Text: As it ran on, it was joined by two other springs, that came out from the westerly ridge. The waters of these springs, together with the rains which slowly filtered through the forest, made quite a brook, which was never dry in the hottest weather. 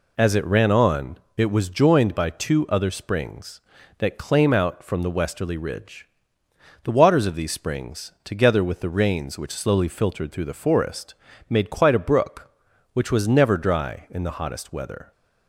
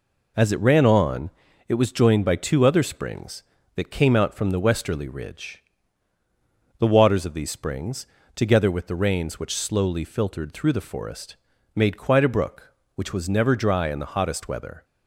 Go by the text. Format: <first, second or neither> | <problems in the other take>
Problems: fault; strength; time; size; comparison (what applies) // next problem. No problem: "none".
second | says "claim" for "came"; at 4.1 s